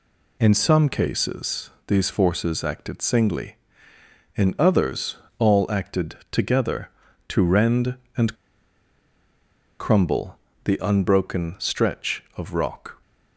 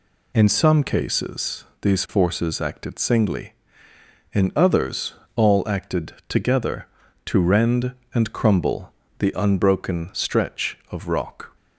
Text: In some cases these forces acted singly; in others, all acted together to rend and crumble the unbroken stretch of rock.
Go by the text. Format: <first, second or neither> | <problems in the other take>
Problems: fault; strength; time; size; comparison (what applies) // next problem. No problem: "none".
second | pauses between "cases" and "these"; slight; at 1.6 s; 0.18 s long; slight in the second // pauses between "acted" and "together"; slight; at 6.1 s; 0.16 s long; slight in the second // pauses between "and" and "crumble"; strong; at 8.3 s; 1.4 s long // pauses between "crumble" and "the"; slight; at 10.3 s; 0.28 s long; slight in the second